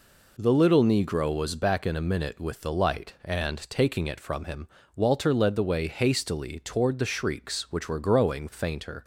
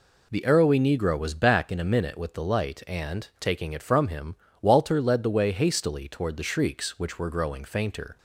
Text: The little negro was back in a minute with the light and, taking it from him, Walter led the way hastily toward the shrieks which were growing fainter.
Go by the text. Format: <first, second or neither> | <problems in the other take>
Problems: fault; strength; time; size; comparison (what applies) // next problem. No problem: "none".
first | says "arrowy" for "little"; at 0.4 s